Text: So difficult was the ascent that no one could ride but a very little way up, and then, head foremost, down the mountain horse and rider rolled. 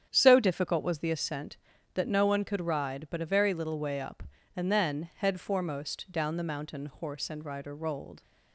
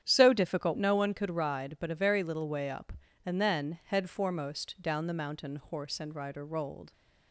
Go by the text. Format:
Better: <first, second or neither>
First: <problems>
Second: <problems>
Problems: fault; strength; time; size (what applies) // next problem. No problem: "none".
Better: first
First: starts louder than the rest; strong; until 1.1 s; 9 dB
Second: starts louder than the rest; strong; until 1.0 s; 9.5 dB // skips "was the ascent that"; at 0.7 s